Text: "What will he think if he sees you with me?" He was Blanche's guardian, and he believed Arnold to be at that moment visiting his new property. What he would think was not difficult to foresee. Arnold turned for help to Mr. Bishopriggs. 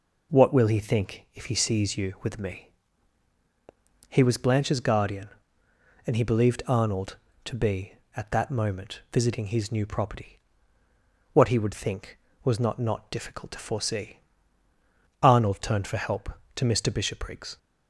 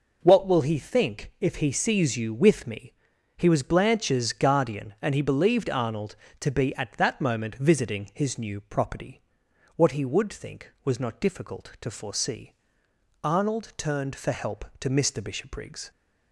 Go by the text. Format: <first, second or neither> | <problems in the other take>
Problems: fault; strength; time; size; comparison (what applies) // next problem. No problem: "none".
second | says "not" twice; at 12.7 s